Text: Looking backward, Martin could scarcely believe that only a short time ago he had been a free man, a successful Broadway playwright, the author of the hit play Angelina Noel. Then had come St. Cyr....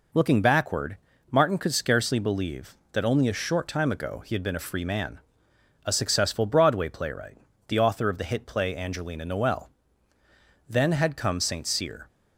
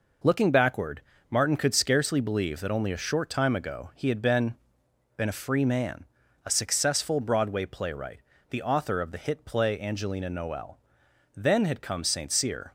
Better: first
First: none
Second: says "been" twice; at 5.1 s

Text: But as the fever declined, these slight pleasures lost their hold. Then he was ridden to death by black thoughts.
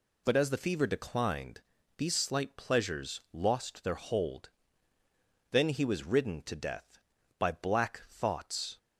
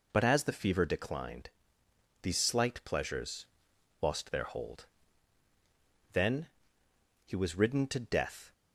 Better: first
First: none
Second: pauses between "pleasures" and "lost"; noticeable; at 3.4 s; 0.56 s long // pauses between "Then" and "he"; noticeable; at 6.4 s; 0.78 s long // stops before "by black thoughts"; at 8.5 s

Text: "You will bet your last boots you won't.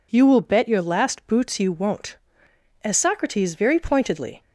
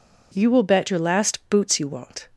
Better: second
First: goes on to say "As Socrates very pointedly"; from 2.8 s on; 1.5 s long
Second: none

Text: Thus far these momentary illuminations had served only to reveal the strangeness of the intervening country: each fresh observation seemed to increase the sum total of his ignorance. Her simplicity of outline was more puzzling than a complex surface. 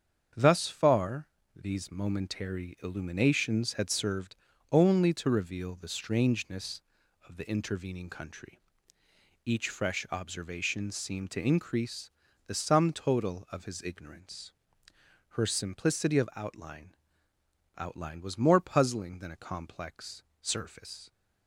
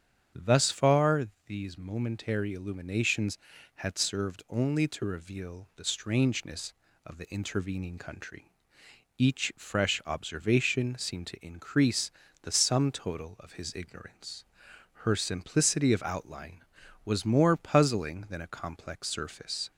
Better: second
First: starts louder than the rest; strong; until 1.6 s; 7.5 dB // pauses between "far" and "these"; slight; at 1.2 s; 0.28 s long // pauses between "served" and "only"; slight; at 4.3 s; 0.34 s long // pauses between "increase" and "the"; slight; at 12.1 s; 0.36 s long // says "outline" twice; at 17.7 s // pauses between "complex" and "surface"; slight; at 20.2 s; 0.18 s long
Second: starts louder than the rest; strong; until 1.5 s; 8 dB // pauses between "far" and "these"; slight; at 1.2 s; 0.20 s long // pauses between "increase" and "the"; slight; at 12.1 s; 0.30 s long

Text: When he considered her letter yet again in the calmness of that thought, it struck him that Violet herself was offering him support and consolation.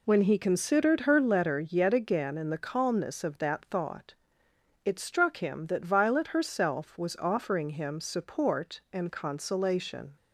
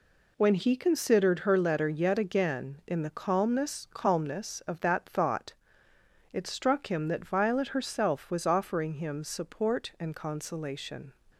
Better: first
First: none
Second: says "calmness" twice; at 3.9 s

